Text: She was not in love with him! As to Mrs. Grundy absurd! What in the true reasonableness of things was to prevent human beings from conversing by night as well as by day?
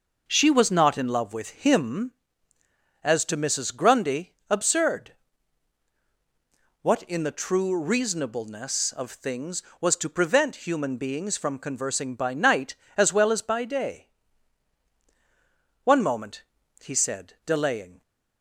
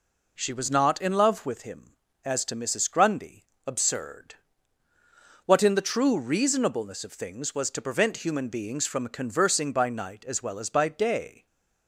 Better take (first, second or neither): second